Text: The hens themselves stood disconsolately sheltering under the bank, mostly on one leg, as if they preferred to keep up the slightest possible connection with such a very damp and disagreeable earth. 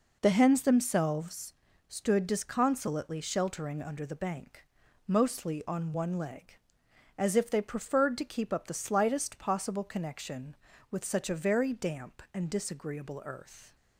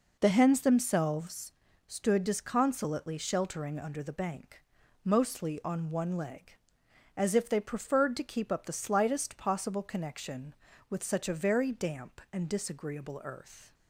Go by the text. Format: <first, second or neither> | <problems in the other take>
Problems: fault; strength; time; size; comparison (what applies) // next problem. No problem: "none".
neither | pauses between "themselves" and "stood"; slight; the same in both